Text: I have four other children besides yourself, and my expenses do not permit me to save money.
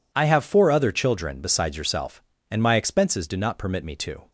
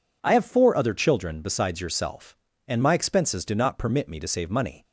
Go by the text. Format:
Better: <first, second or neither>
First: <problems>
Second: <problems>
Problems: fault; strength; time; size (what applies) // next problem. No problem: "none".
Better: second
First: stops before "save money"; at 4.2 s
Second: none